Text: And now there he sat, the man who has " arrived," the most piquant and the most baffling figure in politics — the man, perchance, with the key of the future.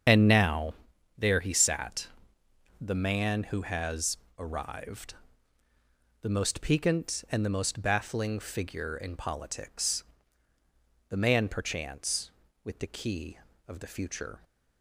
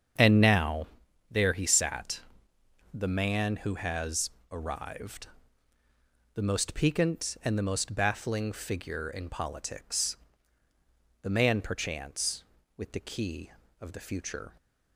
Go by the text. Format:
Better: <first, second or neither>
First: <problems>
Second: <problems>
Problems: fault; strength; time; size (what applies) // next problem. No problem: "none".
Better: second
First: loses the start of "And"; at 0.0 s; 40 ms // starts louder than the rest; strong; until 1.5 s; 7.5 dB // pauses between "now" and "there"; at 0.7 s; 0.44 s long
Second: starts louder than the rest; strong; until 1.6 s; 7.5 dB // pauses between "now" and "there"; at 0.8 s; 0.44 s long